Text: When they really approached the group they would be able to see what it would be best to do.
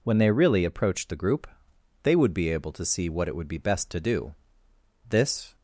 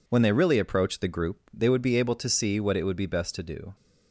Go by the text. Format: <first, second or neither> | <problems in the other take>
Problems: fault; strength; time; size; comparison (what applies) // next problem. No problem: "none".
second | pauses between "group" and "they"; noticeable; at 1.4 s; 0.56 s long // goes on to say "This"; slight; from 5.0 s on; 0.48 s long